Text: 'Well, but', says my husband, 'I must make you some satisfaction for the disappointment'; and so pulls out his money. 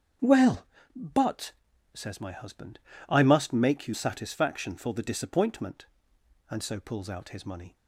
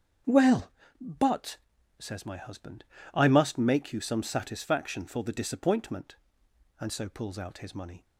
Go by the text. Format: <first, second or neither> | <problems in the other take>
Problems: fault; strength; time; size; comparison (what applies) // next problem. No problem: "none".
second | starts louder than the rest; strong; until 1.5 s; 7.5 dB; strong in the second // skips "some"; at 3.9 s